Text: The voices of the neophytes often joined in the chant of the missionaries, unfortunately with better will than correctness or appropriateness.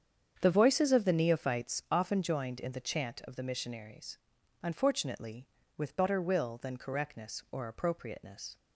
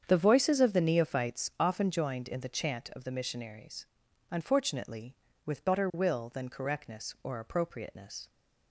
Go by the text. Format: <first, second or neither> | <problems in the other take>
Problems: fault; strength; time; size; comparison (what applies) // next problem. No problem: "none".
neither | starts louder than the rest; strong; the same in both